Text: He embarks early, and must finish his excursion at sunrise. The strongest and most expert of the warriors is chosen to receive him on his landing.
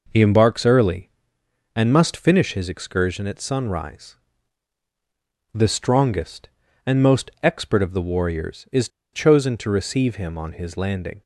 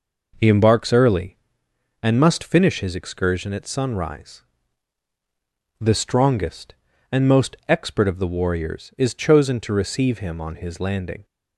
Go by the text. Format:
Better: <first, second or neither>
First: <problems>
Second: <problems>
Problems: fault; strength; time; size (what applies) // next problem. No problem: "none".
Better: second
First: pauses between "is" and "chosen"; slight; at 8.8 s; 0.25 s long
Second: none